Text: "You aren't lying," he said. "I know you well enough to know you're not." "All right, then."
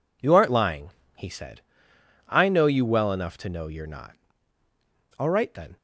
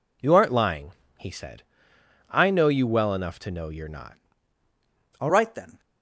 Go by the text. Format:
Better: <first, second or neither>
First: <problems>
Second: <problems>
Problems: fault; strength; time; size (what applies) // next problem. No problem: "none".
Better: first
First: none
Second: changes voice at "right"; from 5.2 s on; 0.6 s long